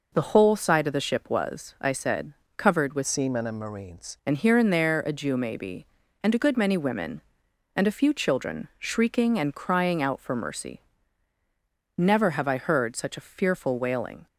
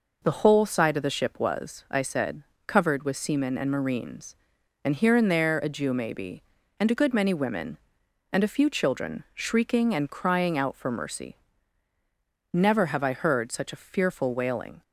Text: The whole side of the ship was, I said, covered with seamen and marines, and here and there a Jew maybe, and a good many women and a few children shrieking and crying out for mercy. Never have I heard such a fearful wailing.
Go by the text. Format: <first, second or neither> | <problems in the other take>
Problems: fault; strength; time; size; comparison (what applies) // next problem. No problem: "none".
second | changes voice from "seamen" to "marines"; from 3.0 to 4.1 s; 1.1 s long